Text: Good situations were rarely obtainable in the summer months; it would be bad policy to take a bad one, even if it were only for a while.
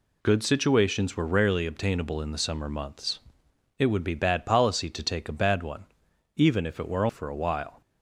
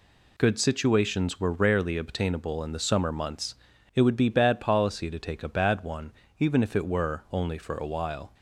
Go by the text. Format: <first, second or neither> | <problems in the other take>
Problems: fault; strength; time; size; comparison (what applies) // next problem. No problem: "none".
second | skips "only"; at 7.0 s